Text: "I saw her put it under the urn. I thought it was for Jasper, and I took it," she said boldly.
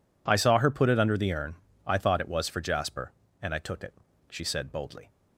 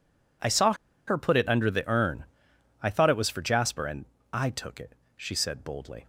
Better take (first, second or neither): first